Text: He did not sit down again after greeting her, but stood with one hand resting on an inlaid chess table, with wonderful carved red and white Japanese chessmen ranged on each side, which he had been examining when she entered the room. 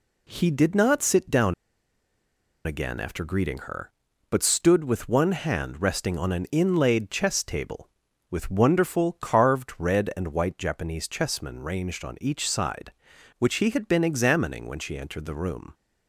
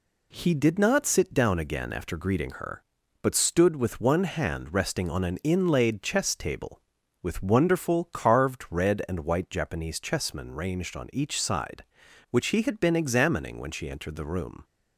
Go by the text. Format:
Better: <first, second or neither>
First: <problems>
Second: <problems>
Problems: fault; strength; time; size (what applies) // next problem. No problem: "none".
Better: second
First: pauses between "down" and "again"; at 1.5 s; 1.1 s long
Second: none